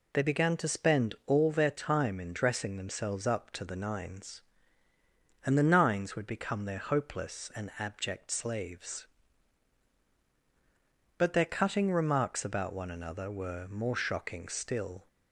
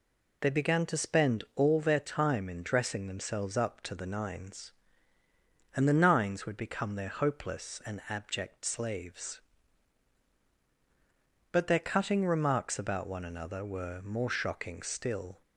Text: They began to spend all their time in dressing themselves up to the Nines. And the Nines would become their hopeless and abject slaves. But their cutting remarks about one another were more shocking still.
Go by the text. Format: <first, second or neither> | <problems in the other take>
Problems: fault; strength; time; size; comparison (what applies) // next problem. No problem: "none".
neither | none